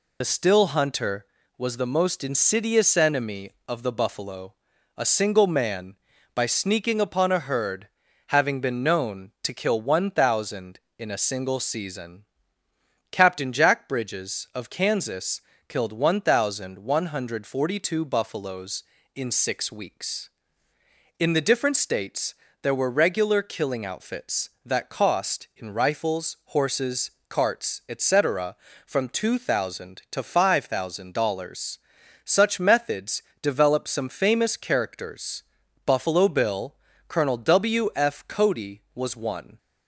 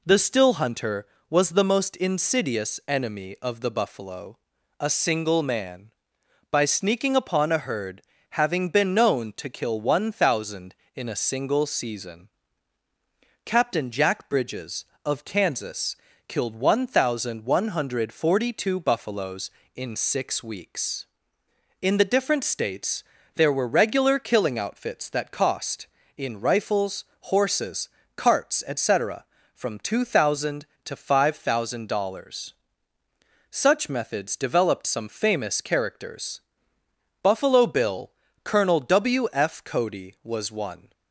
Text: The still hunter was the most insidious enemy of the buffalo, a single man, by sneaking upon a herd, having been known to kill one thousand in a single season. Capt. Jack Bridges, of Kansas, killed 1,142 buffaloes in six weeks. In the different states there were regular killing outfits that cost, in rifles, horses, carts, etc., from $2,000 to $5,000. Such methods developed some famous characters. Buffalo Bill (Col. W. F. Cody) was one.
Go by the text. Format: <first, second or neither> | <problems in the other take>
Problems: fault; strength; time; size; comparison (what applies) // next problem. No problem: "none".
second | loses the start of "The"; at 0.2 s; 50 ms // pauses between "states" and "there"; slight; at 22.3 s; 0.26 s long; slight in the second // pauses between "methods" and "developed"; slight; at 33.2 s; 0.22 s long